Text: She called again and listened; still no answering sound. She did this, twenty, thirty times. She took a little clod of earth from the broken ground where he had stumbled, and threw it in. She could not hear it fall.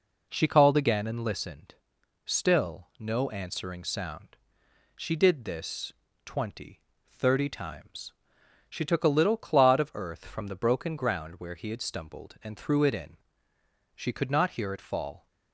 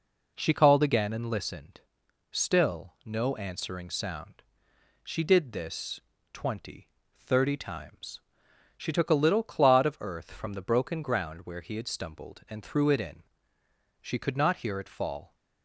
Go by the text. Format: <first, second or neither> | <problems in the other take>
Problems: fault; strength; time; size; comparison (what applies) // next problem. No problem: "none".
neither | none